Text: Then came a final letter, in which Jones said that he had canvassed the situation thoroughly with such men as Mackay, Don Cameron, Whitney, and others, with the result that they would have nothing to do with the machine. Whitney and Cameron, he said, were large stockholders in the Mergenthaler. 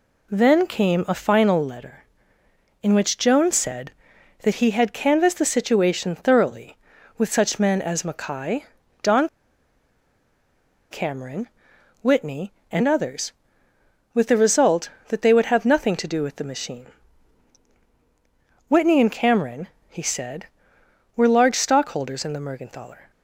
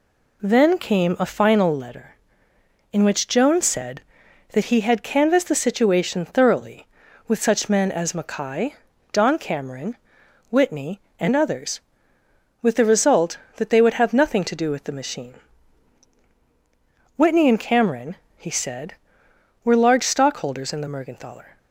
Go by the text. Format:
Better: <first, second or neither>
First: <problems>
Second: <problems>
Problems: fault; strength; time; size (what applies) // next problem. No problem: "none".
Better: second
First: pauses between "Don" and "Cameron"; strong; at 9.2 s; 1.6 s long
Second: none